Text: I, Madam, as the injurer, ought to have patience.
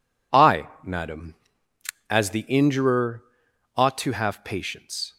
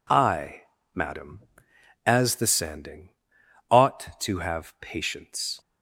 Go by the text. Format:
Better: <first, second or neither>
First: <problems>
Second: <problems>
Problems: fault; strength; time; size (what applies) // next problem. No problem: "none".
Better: first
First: none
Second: says "sanding" for "injurer"; at 2.4 s